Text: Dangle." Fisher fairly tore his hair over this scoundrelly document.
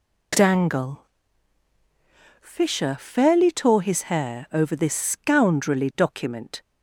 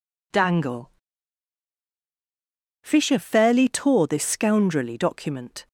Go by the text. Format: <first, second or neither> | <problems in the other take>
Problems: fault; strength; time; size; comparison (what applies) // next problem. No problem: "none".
first | skips "his hair over"; at 4.0 s